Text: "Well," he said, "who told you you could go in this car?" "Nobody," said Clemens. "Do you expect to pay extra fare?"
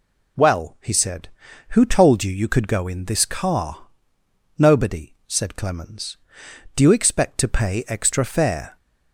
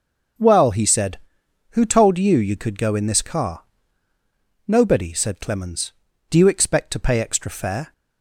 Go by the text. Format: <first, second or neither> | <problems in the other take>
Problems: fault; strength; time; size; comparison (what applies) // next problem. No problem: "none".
neither | none